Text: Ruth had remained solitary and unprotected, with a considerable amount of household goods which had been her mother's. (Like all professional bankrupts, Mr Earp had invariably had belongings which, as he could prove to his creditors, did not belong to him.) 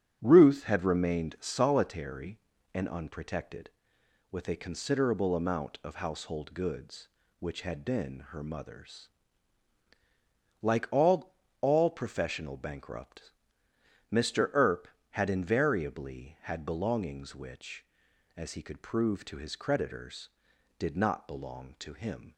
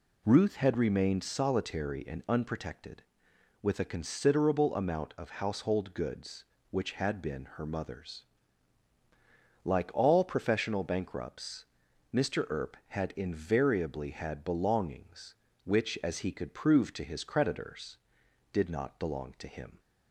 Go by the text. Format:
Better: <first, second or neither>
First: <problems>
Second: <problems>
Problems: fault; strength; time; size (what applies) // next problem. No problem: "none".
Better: second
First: starts louder than the rest; strong; until 1.2 s; 7.5 dB // says "all" twice; at 11.6 s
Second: none